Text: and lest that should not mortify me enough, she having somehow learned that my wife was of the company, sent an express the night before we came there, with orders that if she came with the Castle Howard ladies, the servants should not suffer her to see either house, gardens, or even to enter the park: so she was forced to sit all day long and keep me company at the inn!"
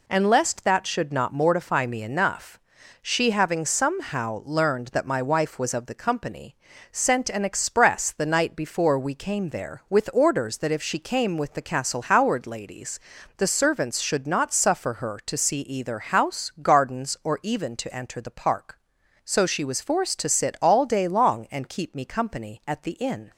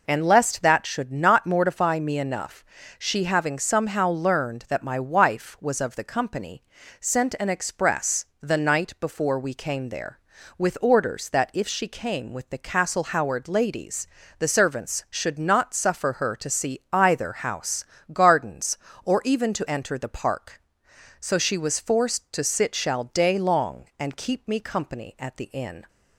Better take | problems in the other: first | pauses between "express" and "the"; slight; at 8.2 s; 0.16 s long // says "shall" for "all"; at 22.7 s

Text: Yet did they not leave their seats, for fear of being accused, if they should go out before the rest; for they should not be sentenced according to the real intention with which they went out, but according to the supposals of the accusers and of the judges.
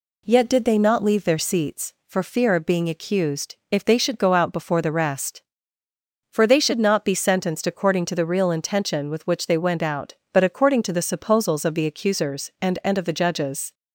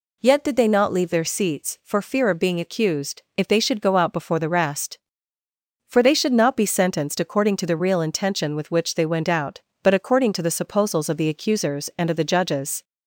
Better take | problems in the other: second | says "and" twice; at 12.8 s

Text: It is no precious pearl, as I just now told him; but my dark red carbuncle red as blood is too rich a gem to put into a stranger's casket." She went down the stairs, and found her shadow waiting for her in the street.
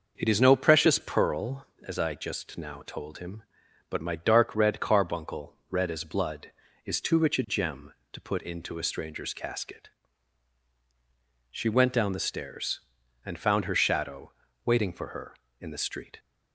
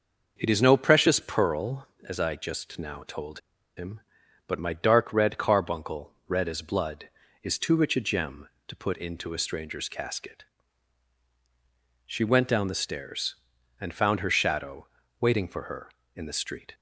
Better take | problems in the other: first | pauses between "told" and "him"; at 3.3 s; 0.37 s long // pauses between "shadow" and "waiting"; slight; at 14.8 s; 0.32 s long; slight in the first

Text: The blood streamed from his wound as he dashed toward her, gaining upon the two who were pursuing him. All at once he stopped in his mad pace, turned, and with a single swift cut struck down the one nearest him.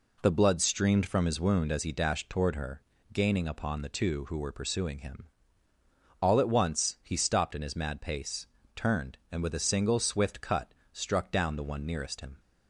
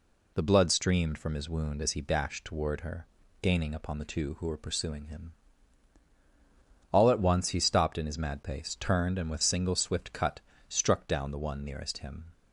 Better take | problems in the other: first | skips "a"; at 9.4 s // pauses between "cut" and "struck"; slight; at 10.3 s; 0.30 s long; slight in the first

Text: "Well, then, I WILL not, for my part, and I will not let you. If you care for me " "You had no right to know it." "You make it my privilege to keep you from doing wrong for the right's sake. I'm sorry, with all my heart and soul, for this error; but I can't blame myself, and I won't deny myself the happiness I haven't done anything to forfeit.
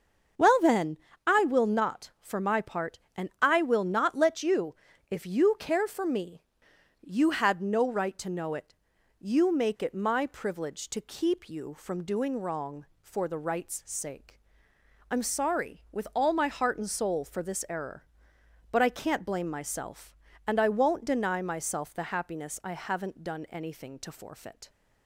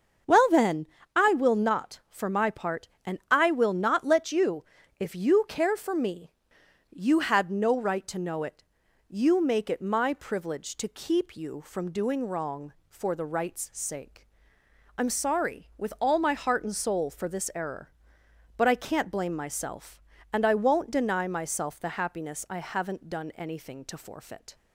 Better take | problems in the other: neither | starts louder than the rest; the same in both

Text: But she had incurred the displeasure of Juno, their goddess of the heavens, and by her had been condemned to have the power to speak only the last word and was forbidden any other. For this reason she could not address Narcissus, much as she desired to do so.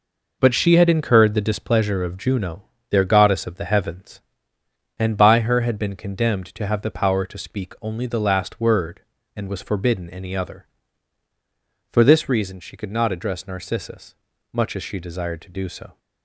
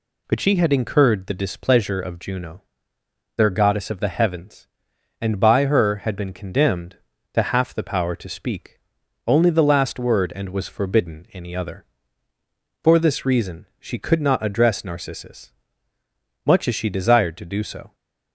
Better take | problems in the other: first | says "half" for "have"; at 7.4 s // pauses between "speak" and "only"; noticeable; at 8.8 s; 0.46 s long // pauses between "reason" and "she"; slight; at 13.6 s; 0.16 s long

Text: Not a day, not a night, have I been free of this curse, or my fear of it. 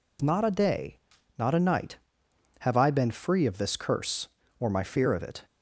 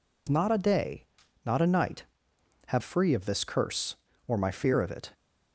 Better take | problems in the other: first | skips "I been"; at 2.8 s

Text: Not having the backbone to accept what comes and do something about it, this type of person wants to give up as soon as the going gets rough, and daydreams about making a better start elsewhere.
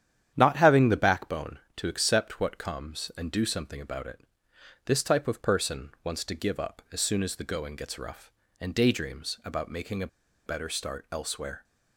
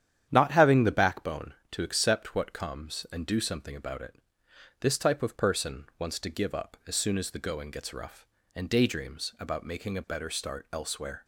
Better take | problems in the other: second | starts louder than the rest; strong; until 1.3 s; 10 dB; strong in the second // pauses between "a" and "better"; at 10.0 s; 0.39 s long

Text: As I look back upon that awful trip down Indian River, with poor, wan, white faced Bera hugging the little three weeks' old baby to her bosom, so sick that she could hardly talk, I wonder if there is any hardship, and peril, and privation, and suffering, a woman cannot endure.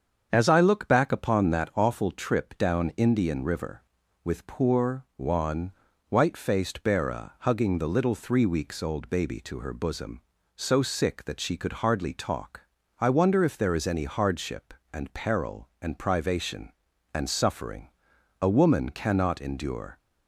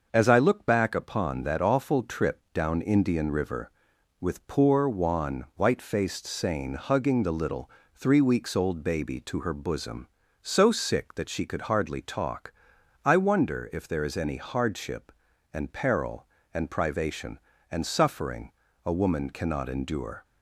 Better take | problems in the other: first | starts louder than the rest; until 1.1 s; 6.5 dB; strong in the first // says "Sane" for "Bera"; at 6.2 s // pauses between "little" and "three"; slight; at 7.6 s; 0.24 s long

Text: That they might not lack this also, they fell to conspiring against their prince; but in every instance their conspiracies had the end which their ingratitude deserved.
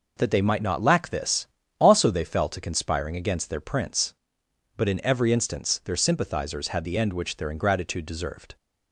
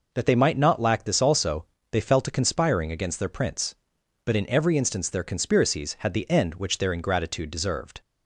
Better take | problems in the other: second | pauses between "this" and "also"; slight; at 1.4 s; 0.34 s long // says "sympathizers" for "conspiracies"; at 5.9 s

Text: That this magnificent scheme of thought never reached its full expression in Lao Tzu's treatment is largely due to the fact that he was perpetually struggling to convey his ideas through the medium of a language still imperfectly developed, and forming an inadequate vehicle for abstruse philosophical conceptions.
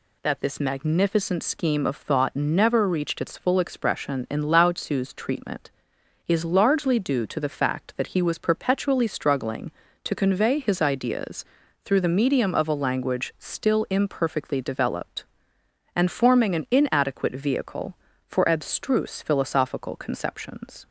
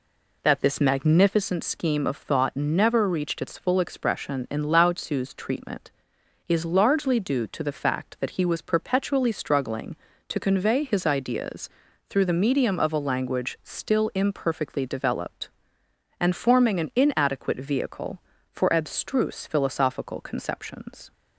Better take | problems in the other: first | starts louder than the rest; slight; until 1.4 s; 3 dB // pauses between "ideas" and "through"; at 11.6 s; 0.40 s long; also in the first

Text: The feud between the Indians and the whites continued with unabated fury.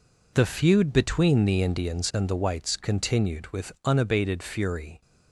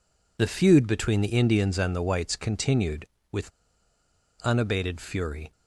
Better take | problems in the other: first | pauses between "with" and "unabated"; noticeable; at 3.5 s; 0.91 s long

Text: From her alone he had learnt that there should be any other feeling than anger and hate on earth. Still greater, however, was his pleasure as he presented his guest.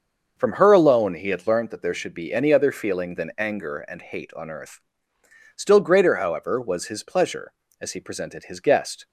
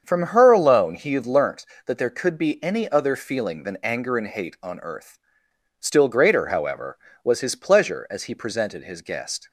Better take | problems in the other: first | starts louder than the rest; strong; until 1.0 s; 7 dB; also in the first // says "could" for "should"; at 2.1 s

